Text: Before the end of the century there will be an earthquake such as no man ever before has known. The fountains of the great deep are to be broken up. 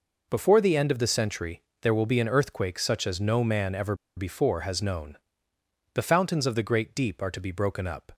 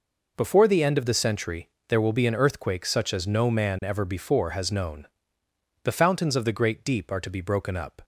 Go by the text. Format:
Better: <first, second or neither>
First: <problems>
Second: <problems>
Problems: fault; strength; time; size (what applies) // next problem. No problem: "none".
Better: second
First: pauses between "century" and "there"; slight; at 1.6 s; 0.18 s long // pauses between "ever" and "before"; slight; at 3.9 s; 0.22 s long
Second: pauses between "century" and "there"; slight; at 1.6 s; 0.18 s long